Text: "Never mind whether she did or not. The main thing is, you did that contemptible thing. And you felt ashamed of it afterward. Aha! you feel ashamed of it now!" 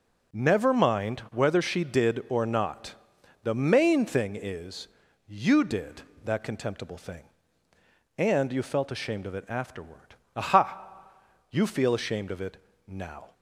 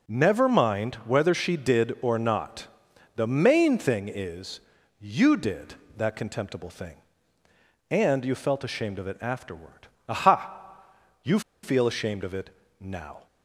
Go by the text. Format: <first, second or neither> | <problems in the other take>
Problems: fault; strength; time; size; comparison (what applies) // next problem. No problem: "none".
first | pauses between "you" and "feel"; slight; at 11.3 s; 0.23 s long // pauses between "it" and "now"; slight; at 12.5 s; 0.30 s long; slight in the first